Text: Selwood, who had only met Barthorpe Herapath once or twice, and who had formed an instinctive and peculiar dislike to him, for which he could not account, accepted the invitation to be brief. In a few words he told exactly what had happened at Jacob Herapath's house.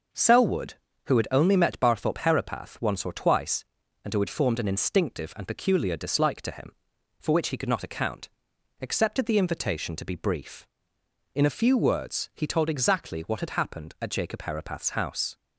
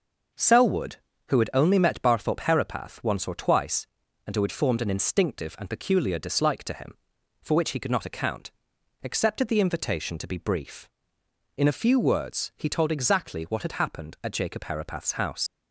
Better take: first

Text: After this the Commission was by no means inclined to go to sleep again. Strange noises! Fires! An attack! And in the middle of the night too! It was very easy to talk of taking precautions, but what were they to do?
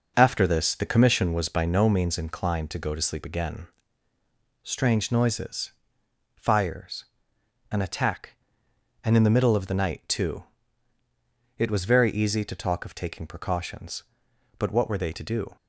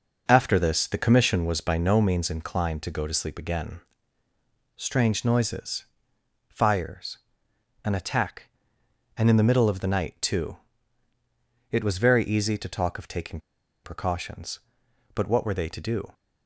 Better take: first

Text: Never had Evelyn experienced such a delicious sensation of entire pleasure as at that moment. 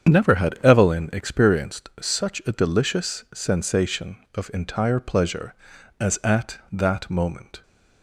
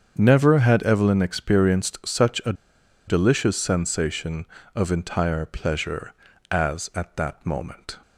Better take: first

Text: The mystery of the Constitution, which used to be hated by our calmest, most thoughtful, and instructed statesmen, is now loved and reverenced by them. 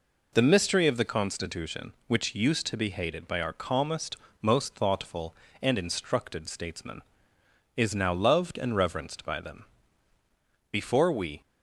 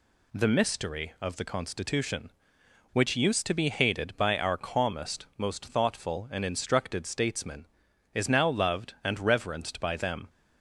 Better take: second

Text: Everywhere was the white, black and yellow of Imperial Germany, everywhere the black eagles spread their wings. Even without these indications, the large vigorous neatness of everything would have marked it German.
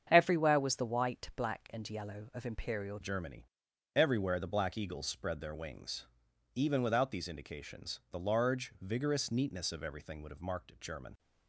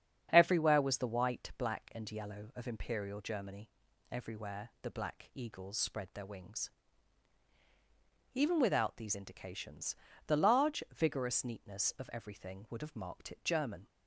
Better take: second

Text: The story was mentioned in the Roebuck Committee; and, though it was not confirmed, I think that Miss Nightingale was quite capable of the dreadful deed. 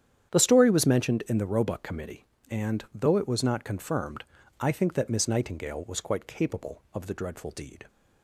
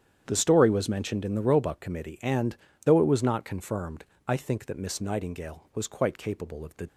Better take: first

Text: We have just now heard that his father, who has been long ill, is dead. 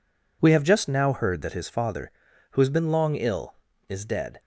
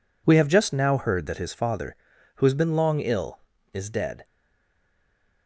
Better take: first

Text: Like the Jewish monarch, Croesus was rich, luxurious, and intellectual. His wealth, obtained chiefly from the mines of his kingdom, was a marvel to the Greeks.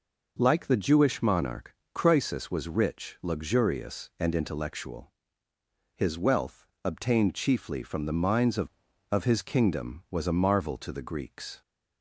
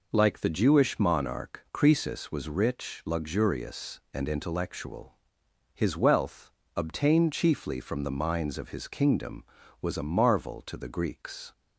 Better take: second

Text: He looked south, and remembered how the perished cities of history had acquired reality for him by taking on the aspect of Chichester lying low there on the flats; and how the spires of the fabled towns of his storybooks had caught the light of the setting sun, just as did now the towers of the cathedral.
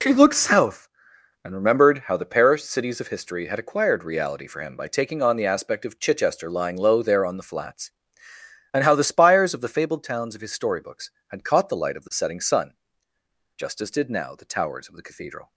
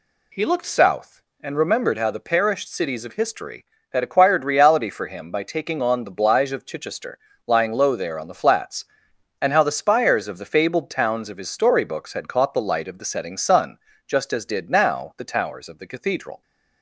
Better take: first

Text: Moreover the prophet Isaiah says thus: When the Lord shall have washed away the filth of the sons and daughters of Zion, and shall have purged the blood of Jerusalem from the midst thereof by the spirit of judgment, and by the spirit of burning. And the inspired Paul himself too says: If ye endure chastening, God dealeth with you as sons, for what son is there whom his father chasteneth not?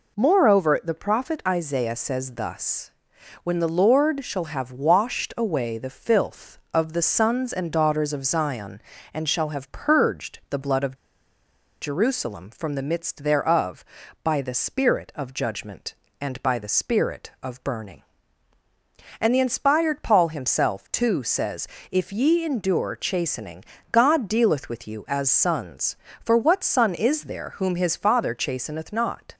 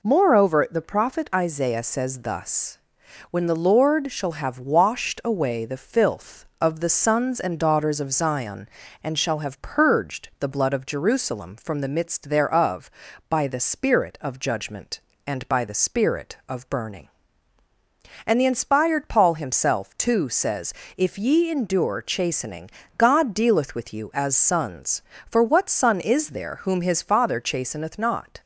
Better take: second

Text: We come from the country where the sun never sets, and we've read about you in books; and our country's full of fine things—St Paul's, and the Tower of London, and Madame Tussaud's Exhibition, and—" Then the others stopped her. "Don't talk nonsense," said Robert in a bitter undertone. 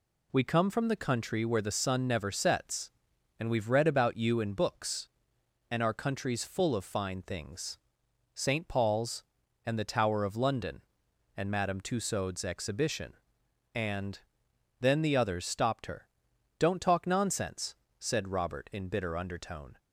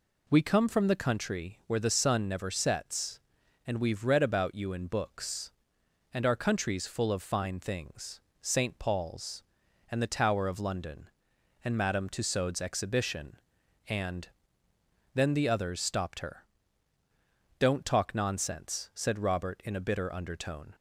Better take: second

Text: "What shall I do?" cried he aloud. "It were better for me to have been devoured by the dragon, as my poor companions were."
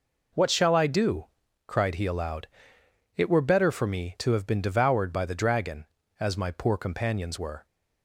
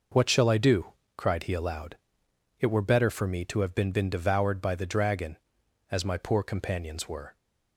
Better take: first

